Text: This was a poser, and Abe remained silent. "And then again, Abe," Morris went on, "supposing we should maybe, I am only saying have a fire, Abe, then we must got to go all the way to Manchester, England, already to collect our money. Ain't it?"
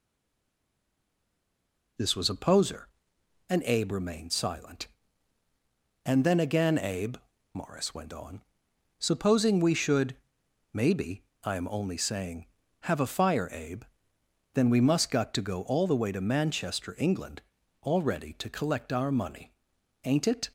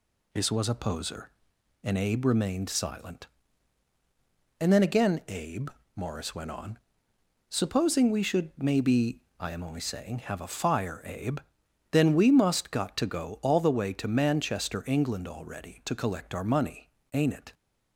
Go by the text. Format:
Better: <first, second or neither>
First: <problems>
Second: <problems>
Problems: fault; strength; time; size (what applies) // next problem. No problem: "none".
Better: second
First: stays silent before the first word; noticeable; until 1.9 s; 1.9 s long // pauses between "should" and "maybe"; noticeable; at 10.1 s; 0.60 s long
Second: none